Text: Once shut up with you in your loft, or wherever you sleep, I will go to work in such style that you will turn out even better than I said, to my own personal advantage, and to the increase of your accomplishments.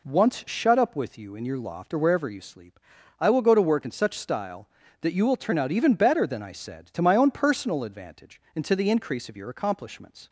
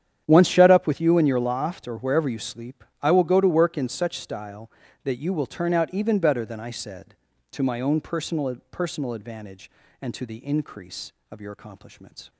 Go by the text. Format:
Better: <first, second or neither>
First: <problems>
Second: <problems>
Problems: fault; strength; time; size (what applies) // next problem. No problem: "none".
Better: first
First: none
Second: starts louder than the rest; strong; until 1.2 s; 9.5 dB // says "personal" twice; at 8.6 s